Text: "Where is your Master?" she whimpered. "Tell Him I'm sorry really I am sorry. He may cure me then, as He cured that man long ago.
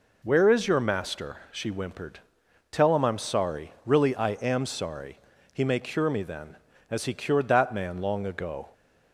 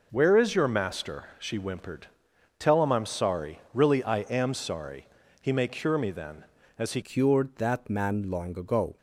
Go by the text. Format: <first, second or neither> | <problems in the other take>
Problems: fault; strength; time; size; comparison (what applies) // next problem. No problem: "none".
first | changes voice at "cured"; from 7.0 s on; 1.9 s long